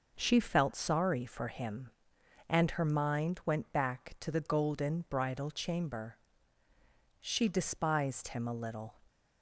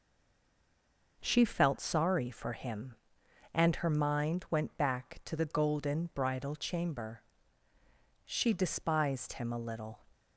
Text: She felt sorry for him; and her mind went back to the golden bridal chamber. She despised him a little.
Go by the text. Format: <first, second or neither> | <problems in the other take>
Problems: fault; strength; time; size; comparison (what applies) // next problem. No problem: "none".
first | stays silent before the first word; noticeable; until 1.1 s; 1.1 s long